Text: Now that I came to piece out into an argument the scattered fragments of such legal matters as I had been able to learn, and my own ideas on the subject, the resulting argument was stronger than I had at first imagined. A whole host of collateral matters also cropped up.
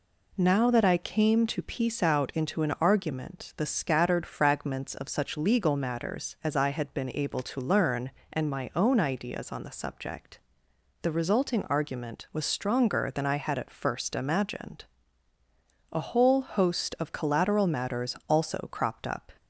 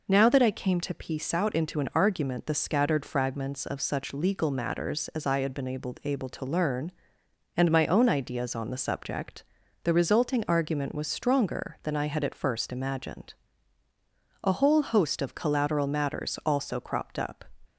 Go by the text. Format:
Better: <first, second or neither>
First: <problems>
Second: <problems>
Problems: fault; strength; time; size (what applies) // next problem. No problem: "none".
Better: first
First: none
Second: says "able" twice; at 6.0 s